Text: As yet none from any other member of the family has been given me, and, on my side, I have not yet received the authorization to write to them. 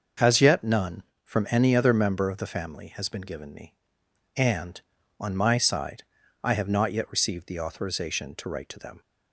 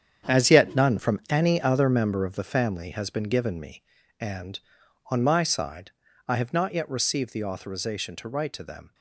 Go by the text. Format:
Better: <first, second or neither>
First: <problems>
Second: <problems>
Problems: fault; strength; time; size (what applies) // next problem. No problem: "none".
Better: first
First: starts louder than the rest; until 1.4 s; 6 dB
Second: gets quieter; strong; throughout; 11 dB // starts louder than the rest; strong; until 1.3 s; 8 dB